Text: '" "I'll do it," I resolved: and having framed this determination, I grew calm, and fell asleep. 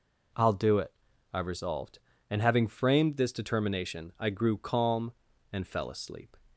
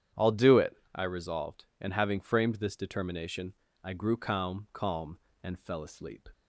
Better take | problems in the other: first | starts louder than the rest; strong; until 1.3 s; 9.5 dB // says "calm" twice; at 4.7 s

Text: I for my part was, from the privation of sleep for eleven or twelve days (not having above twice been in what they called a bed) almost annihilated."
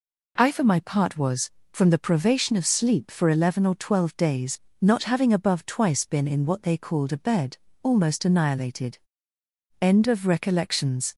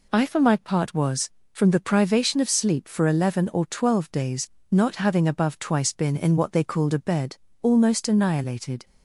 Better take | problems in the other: second | goes on to say "END OF RECOLLECTIONS"; from 9.8 s on; 1.3 s long

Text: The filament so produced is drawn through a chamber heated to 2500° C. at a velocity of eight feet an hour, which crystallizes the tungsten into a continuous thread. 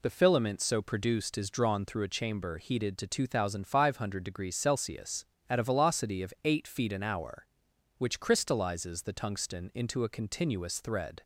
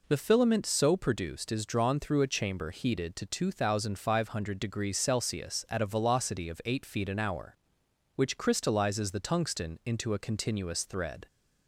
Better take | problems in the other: neither | none

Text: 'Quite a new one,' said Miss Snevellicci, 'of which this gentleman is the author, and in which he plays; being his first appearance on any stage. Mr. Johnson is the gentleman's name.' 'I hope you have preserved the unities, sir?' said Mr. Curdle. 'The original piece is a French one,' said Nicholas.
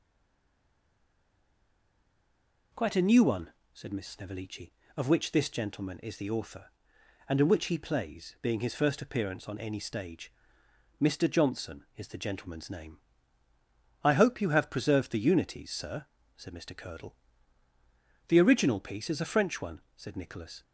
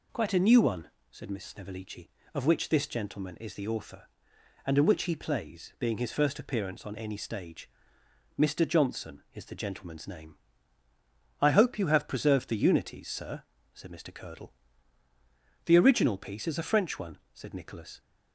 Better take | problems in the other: second | stays silent before the first word; strong; until 2.7 s; 2.7 s long

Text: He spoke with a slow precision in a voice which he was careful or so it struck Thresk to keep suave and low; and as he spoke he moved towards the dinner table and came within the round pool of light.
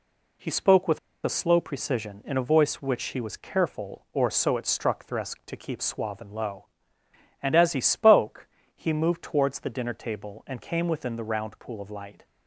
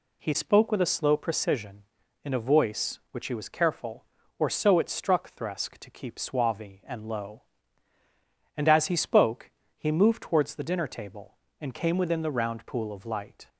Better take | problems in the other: second | pauses between "with" and "a"; slight; at 0.9 s; 0.27 s long // pauses between "spoke" and "he"; slight; at 8.4 s; 0.28 s long; slight in the second

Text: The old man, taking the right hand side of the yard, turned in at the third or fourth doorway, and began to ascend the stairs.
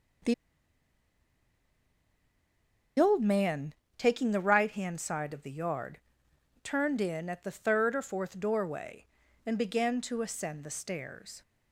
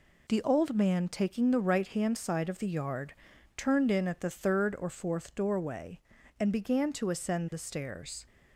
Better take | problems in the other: second | pauses between "The" and "old"; strong; at 0.3 s; 2.6 s long

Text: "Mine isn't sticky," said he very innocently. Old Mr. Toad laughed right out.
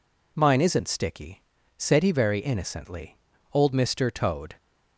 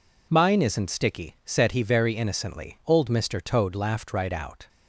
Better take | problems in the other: second | stops before "laughed right out"; at 4.5 s

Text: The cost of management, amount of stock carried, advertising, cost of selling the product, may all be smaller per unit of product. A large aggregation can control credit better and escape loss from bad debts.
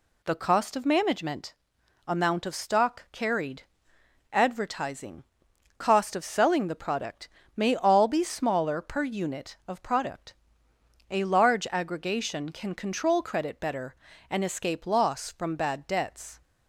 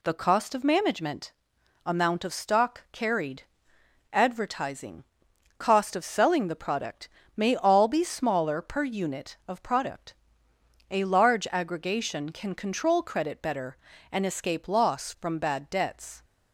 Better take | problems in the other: neither | none

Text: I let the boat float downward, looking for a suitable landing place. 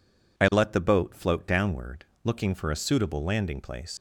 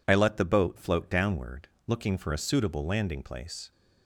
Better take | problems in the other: second | leaves "place" unfinished; at 3.9 s; 120 ms

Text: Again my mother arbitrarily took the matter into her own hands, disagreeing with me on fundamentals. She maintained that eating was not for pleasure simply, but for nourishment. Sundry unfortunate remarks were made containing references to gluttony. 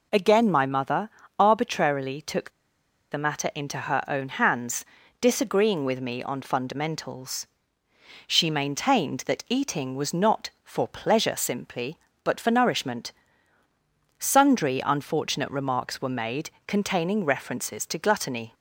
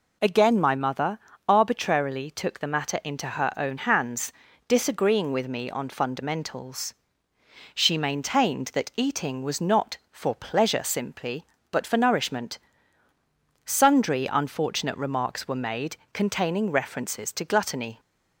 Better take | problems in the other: second | pauses between "mother" and "arbitrarily"; slight; at 1.0 s; 0.28 s long; slight in the second // pauses between "took" and "the"; noticeable; at 2.4 s; 0.61 s long // pauses between "made" and "containing"; slight; at 16.4 s; 0.16 s long; slight in the second

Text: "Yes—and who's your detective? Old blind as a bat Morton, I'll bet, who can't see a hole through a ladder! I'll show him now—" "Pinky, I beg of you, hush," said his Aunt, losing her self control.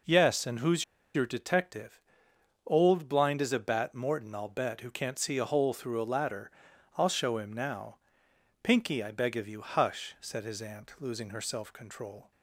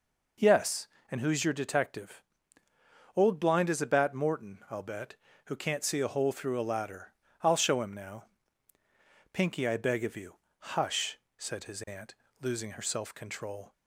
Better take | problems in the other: second | pauses between "who's" and "your"; slight; at 0.8 s; 0.30 s long

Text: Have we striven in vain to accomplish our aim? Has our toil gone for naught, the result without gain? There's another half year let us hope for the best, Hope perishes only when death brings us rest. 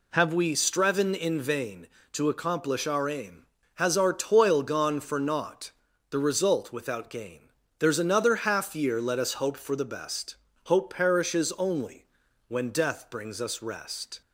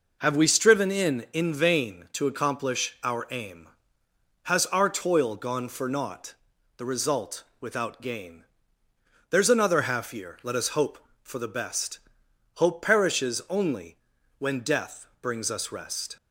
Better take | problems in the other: first | says "in" twice; at 1.3 s // pauses between "result" and "without"; slight; at 7.4 s; 0.18 s long // pauses between "only" and "when"; at 13.9 s; 0.42 s long; also in the first // pauses between "death" and "brings"; slight; at 15.0 s; 0.16 s long

